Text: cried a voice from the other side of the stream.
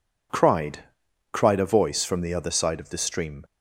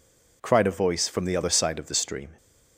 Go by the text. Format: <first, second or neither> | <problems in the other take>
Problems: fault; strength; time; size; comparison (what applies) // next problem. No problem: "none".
second | says "cried" twice; at 1.3 s